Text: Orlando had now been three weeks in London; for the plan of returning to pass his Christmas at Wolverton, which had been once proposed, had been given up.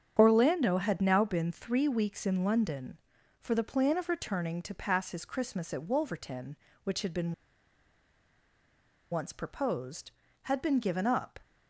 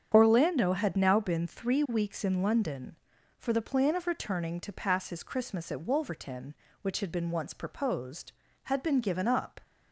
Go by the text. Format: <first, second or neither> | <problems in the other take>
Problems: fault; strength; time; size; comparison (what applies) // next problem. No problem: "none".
second | starts louder than the rest; strong; until 1.2 s; 8 dB; strong in the second // pauses between "been" and "once"; strong; at 7.3 s; 1.7 s long